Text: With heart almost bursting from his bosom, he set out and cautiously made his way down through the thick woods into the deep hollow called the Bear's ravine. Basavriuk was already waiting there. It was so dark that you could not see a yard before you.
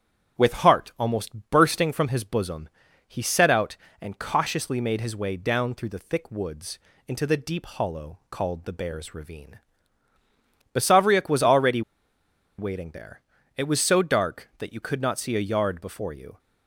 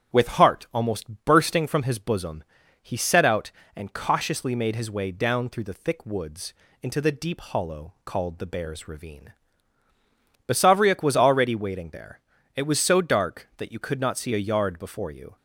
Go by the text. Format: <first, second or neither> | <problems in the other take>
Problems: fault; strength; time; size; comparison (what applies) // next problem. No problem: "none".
second | starts louder than the rest; strong; until 1.4 s; 8.5 dB; strong in the second // pauses between "woods" and "into"; slight; at 6.7 s; 0.30 s long; slight in the second // pauses between "already" and "waiting"; noticeable; at 11.8 s; 0.76 s long